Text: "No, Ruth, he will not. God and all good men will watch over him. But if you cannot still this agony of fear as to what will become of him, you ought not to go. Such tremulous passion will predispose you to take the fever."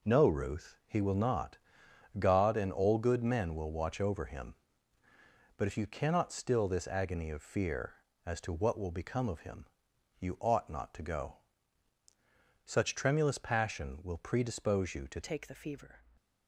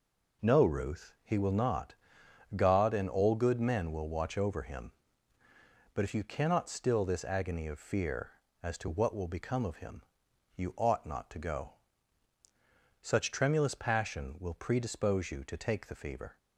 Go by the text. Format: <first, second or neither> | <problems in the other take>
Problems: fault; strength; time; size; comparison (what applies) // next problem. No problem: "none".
second | changes voice at "take"; from 15.2 s on; 0.8 s long